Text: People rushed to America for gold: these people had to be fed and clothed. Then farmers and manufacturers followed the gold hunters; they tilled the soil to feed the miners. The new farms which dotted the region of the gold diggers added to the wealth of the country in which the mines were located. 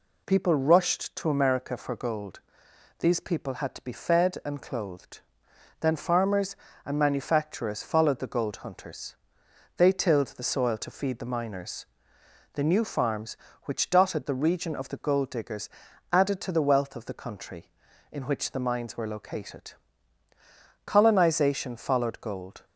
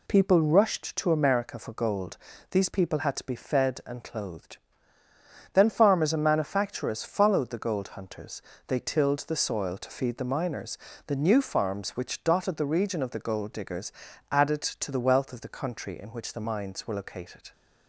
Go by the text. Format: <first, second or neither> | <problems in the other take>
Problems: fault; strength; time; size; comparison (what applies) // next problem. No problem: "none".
second | pauses between "diggers" and "added"; at 15.6 s; 0.42 s long; also in the second // goes on to say "Colonization followed gold"; strong; from 20.8 s on; 1.8 s long